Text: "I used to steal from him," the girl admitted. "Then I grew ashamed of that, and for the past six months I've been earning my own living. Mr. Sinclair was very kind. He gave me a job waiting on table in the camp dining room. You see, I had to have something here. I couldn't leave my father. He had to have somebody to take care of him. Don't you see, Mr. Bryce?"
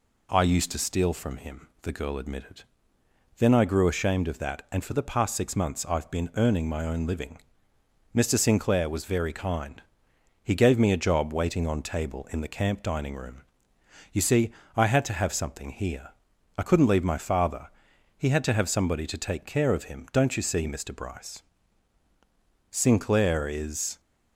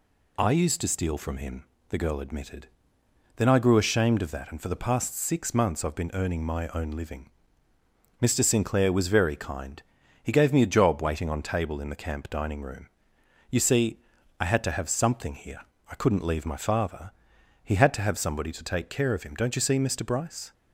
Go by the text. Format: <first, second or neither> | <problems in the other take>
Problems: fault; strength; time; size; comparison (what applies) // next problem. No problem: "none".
second | goes on to say "Sinclair is"; noticeable; from 22.6 s on; 1.3 s long